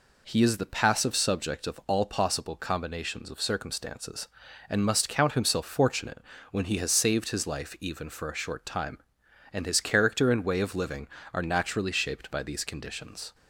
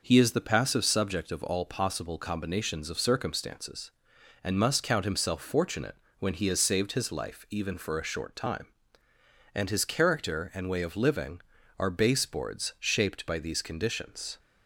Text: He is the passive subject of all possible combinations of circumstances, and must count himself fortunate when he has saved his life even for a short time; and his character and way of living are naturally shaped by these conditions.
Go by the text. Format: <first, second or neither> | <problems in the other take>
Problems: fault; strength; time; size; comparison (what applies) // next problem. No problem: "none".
first | pauses between "fortunate" and "when"; slight; at 5.9 s; 0.24 s long; slight in the first // says "baseboards" for "naturally"; at 11.8 s